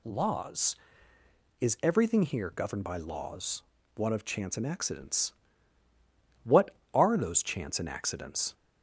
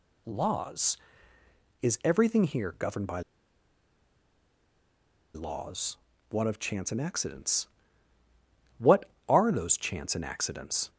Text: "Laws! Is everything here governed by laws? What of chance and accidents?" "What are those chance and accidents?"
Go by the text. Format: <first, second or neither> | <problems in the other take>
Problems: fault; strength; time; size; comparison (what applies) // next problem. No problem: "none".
first | pauses between "by" and "laws"; strong; at 3.2 s; 2.1 s long